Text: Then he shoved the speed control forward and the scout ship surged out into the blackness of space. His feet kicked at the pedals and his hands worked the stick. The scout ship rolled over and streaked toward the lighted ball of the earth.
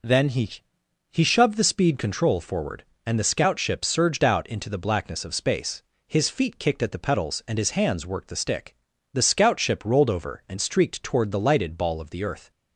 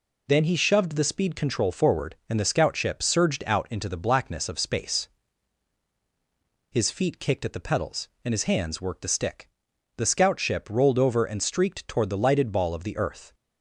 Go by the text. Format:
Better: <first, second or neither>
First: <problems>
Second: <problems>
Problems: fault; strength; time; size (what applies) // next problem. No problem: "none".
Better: second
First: says "he" twice; at 1.1 s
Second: none